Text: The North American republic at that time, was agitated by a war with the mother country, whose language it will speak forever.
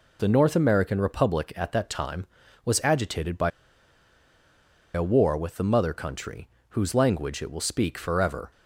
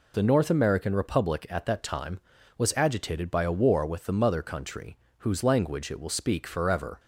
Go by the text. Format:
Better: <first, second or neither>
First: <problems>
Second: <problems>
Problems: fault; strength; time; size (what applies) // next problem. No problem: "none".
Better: second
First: pauses between "by" and "a"; strong; at 3.4 s; 1.4 s long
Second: none